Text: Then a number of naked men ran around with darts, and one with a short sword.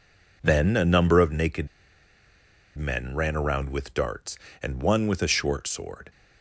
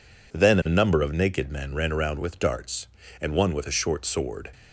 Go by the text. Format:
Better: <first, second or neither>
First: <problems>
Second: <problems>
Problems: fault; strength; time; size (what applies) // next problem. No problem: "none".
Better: second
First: pauses between "naked" and "men"; at 1.6 s; 1.1 s long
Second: none